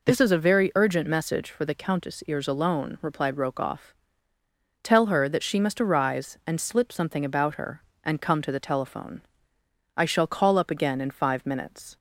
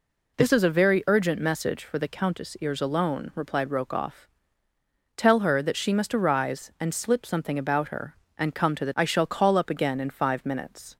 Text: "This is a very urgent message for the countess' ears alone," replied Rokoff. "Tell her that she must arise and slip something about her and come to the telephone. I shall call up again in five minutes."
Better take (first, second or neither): first